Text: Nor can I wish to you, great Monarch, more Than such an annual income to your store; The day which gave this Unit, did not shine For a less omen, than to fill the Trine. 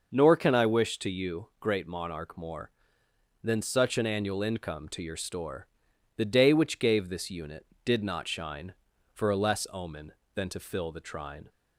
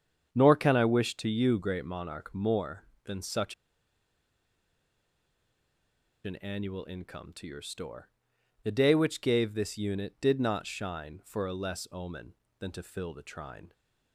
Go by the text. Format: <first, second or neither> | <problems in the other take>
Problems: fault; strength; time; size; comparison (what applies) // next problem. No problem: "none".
first | starts louder than the rest; strong; until 1.3 s; 7.5 dB // pauses between "such" and "an"; strong; at 3.5 s; 2.7 s long